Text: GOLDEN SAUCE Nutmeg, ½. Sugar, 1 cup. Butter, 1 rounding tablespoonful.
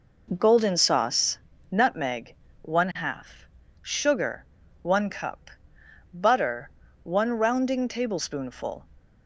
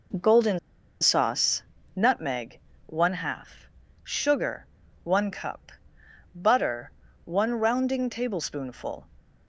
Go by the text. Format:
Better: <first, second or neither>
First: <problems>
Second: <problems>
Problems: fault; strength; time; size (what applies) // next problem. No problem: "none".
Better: first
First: pauses between "SAUCE" and "Nutmeg"; slight; at 1.3 s; 0.32 s long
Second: pauses between "GOLDEN" and "SAUCE"; at 0.5 s; 0.42 s long // pauses between "SAUCE" and "Nutmeg"; slight; at 1.6 s; 0.32 s long